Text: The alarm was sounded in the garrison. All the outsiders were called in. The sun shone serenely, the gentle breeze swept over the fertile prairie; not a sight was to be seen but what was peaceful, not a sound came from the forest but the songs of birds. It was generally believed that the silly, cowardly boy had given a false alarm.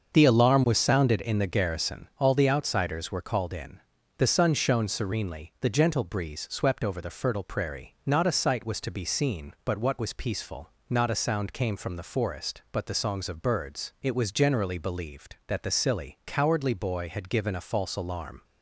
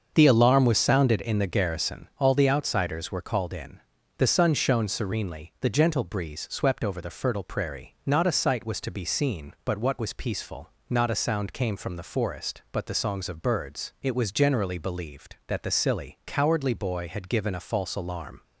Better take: neither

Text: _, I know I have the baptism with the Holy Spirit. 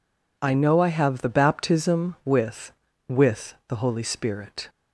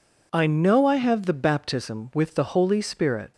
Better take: second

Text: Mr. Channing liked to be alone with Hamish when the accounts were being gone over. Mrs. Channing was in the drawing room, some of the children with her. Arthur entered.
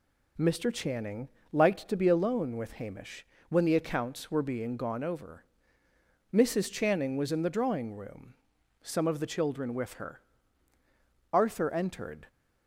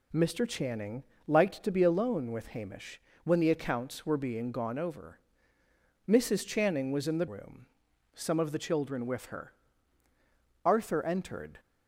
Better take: first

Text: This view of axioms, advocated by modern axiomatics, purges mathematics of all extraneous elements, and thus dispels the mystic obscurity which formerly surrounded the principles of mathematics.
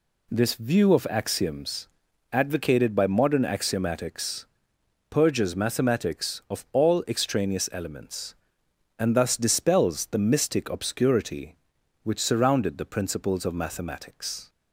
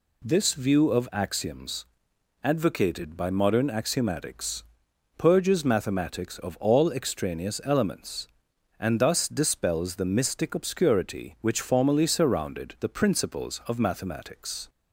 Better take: second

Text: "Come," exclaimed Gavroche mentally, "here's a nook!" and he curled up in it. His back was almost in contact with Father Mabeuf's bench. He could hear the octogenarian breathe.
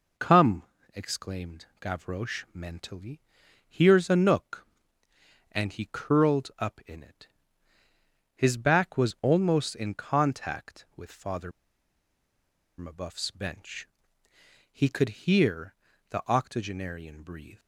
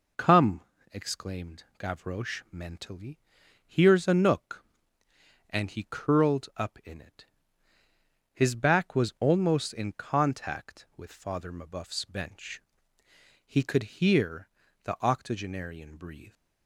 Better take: second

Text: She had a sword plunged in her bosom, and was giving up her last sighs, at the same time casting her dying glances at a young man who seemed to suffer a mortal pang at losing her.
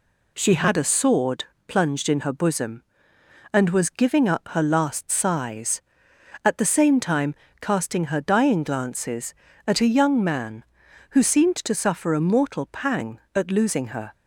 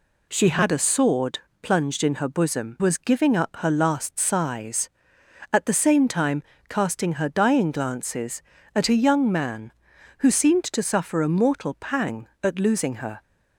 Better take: first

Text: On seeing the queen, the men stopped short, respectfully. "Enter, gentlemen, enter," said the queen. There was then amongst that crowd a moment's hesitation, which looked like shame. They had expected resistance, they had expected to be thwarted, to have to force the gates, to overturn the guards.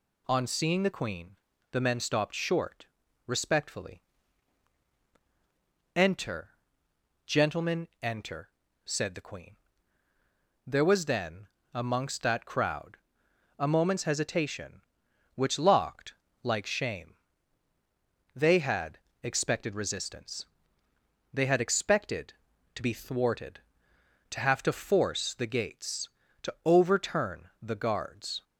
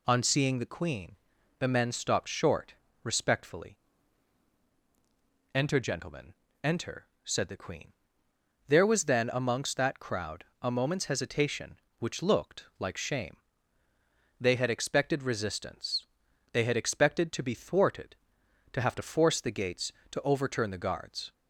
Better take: second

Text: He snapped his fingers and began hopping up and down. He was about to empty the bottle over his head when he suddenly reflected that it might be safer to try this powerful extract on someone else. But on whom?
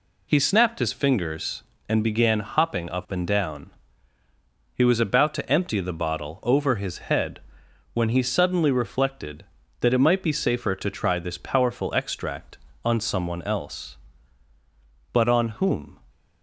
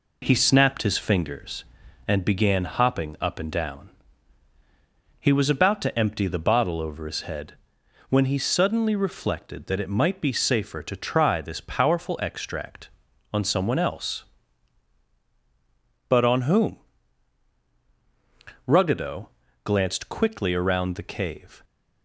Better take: first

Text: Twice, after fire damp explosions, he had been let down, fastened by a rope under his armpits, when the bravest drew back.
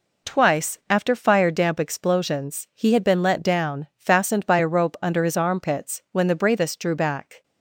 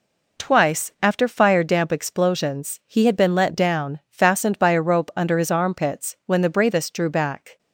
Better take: neither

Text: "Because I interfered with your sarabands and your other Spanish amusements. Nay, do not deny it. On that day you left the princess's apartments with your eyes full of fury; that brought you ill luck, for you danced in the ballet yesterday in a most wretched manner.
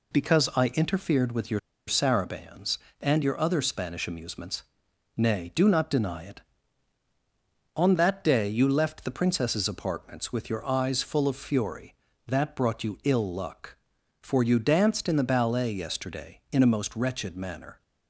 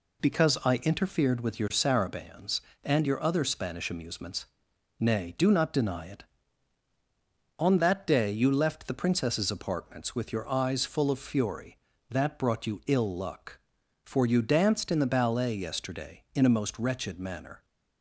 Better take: second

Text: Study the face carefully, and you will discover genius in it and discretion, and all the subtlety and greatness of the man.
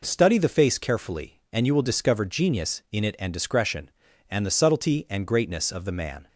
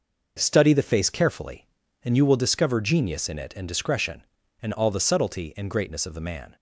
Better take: second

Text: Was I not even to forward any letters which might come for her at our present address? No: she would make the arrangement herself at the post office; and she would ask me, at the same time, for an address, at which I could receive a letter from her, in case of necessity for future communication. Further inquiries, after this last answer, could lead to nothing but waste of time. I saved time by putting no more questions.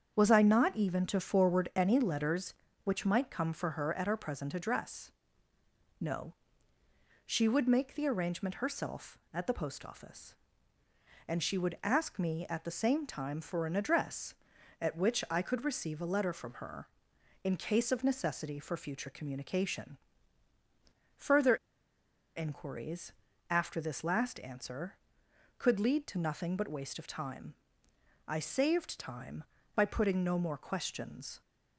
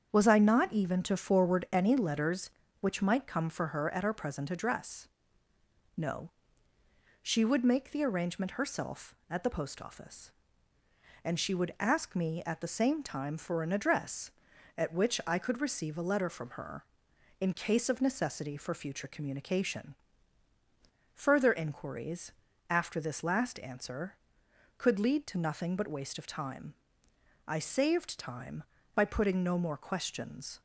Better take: second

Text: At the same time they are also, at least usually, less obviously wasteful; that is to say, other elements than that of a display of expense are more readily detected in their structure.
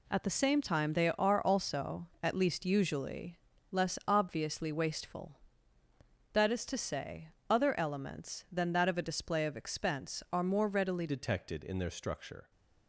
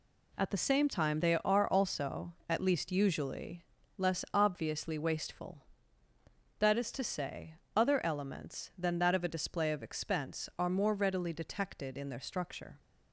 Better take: second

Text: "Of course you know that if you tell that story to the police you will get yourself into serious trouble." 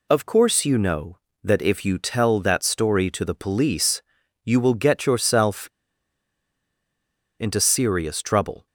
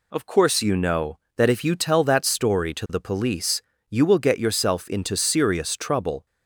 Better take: second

